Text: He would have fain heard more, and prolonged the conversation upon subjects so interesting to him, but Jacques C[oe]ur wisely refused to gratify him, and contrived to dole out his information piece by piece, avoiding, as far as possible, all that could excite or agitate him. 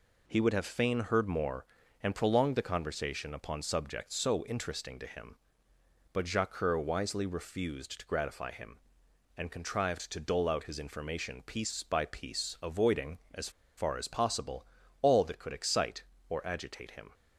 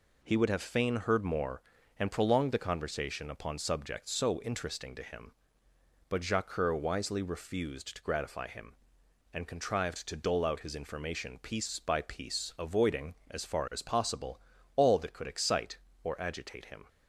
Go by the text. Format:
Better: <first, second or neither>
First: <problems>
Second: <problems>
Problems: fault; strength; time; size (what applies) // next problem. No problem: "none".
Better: second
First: pauses between "as" and "far"; slight; at 13.4 s; 0.27 s long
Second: none